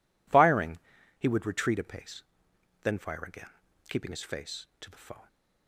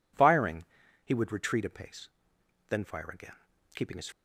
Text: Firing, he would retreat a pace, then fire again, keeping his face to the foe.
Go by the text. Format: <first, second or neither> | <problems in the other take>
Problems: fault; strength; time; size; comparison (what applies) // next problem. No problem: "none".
first | stops before "face to the foe"; at 4.1 s